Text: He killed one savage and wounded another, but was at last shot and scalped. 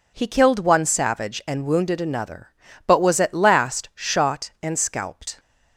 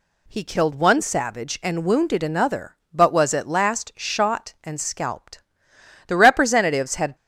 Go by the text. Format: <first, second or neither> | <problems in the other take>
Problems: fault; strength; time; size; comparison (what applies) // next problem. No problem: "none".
first | goes on to say "The representatives had"; noticeable; from 6.0 s on; 1.0 s long